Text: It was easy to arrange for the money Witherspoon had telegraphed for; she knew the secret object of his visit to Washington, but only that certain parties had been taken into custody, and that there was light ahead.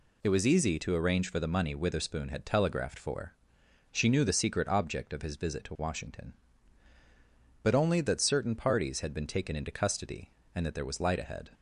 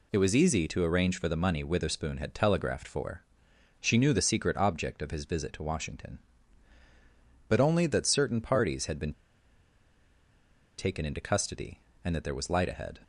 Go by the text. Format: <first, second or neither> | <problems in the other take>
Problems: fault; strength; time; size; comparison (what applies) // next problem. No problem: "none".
first | pauses between "been" and "taken"; strong; at 9.1 s; 1.6 s long